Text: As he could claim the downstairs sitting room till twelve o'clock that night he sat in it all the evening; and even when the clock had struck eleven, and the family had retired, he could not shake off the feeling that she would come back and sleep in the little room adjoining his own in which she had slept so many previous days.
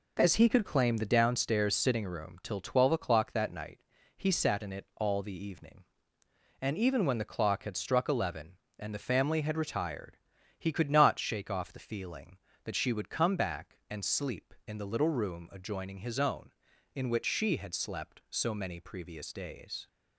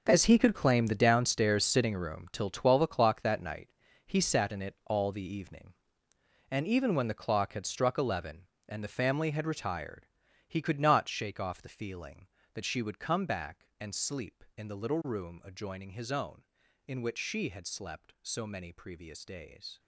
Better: first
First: pauses between "night" and "he"; at 3.7 s; 0.38 s long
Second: gets quieter; strong; throughout; 14 dB // pauses between "night" and "he"; at 3.6 s; 0.38 s long

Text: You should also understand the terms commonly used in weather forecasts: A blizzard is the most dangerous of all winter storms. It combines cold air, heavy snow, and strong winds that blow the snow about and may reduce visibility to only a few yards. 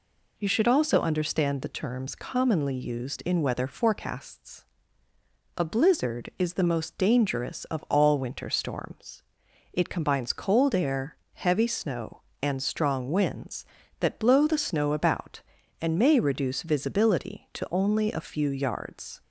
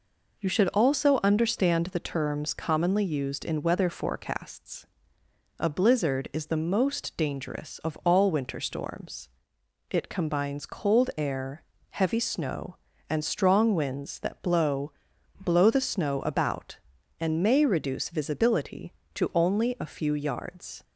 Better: first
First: none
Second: says "blow" twice; at 15.3 s

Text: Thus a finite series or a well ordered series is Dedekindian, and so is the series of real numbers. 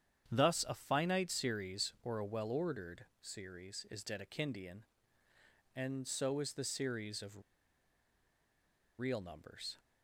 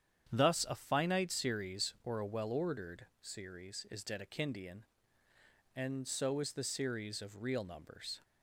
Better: second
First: starts louder than the rest; strong; until 1.3 s; 9 dB // pauses between "ordered" and "series"; slight; at 3.0 s; 0.16 s long // pauses between "of" and "real"; strong; at 7.4 s; 1.5 s long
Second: starts louder than the rest; strong; until 1.3 s; 9 dB // pauses between "ordered" and "series"; slight; at 3.0 s; 0.15 s long

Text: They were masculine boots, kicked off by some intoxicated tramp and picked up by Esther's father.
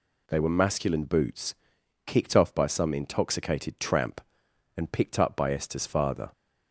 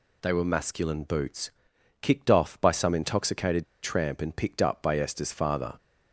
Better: first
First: none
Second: pauses between "intoxicated" and "tramp"; slight; at 3.6 s; 0.18 s long

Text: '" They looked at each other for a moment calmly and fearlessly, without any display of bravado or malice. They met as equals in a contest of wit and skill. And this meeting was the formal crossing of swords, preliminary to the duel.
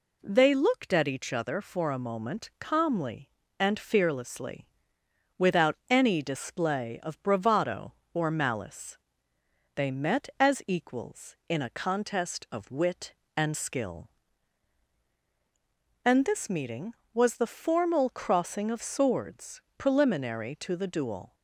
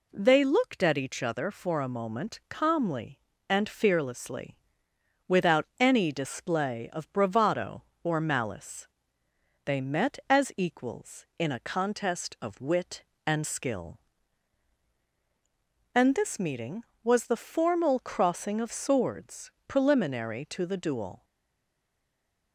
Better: first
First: none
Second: stays silent after the last word; noticeable; from 21.2 s on; 1.3 s long

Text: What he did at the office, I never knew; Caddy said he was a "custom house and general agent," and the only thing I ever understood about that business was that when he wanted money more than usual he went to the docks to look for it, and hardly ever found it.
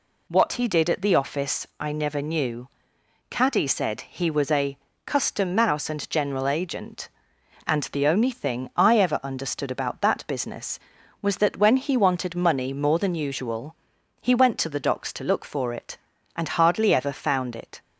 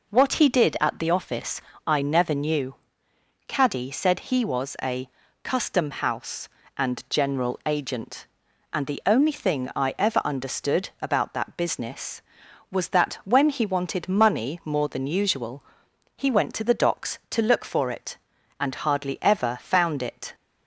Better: second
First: pauses between "a" and "custom"; slight; at 4.7 s; 0.26 s long // says "mouse" for "house"; at 5.5 s // pauses between "usual" and "he"; noticeable; at 13.7 s; 0.46 s long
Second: pauses between "a" and "custom"; slight; at 5.0 s; 0.33 s long // pauses between "usual" and "he"; noticeable; at 15.6 s; 0.54 s long

